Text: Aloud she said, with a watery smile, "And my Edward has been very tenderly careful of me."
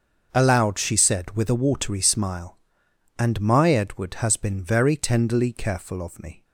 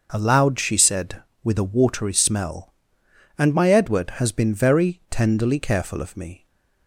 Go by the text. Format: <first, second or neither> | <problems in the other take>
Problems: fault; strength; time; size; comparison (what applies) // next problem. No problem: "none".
first | starts louder than the rest; until 1.1 s; 6 dB; also in the first // says "smell" for "smile"; at 2.1 s